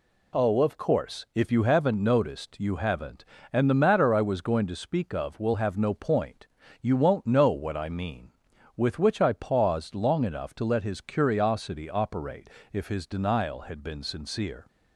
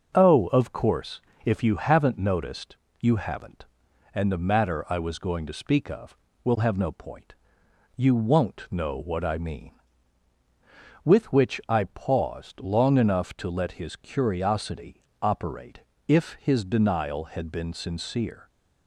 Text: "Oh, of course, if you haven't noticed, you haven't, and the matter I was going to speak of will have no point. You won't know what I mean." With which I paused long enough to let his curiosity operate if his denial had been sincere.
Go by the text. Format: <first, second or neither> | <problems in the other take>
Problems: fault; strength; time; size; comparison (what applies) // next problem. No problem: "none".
first | starts louder than the rest; noticeable; until 1.7 s; 6 dB // pauses between "curiosity" and "operate"; slight; at 15.0 s; 0.22 s long // pauses between "operate" and "if"; slight; at 15.7 s; 0.30 s long; slight in the first